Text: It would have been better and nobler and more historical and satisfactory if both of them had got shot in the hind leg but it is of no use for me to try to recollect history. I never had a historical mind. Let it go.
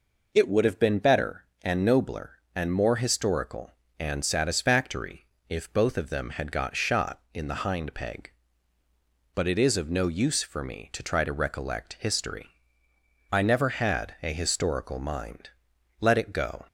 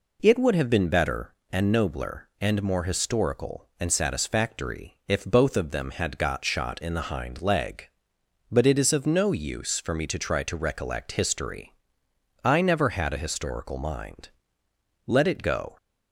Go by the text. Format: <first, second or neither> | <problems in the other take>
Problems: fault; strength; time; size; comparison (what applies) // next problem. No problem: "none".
second | pauses between "satisfactory" and "if"; slight; at 5.2 s; 0.24 s long // says "peg" for "leg"; at 7.9 s